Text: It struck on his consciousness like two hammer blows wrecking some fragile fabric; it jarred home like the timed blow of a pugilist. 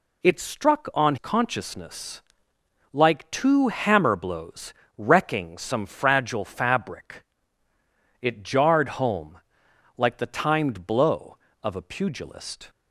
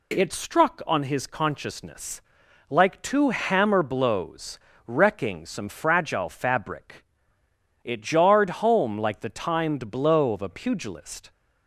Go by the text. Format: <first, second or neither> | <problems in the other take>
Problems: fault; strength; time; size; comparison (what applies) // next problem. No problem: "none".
second | skips "his"; at 1.1 s // pauses between "consciousness" and "like"; noticeable; at 2.2 s; 0.70 s long; noticeable in the second // pauses between "blows" and "wrecking"; slight; at 4.7 s; 0.24 s long; slight in the second // pauses between "home" and "like"; noticeable; at 9.3 s; 0.58 s long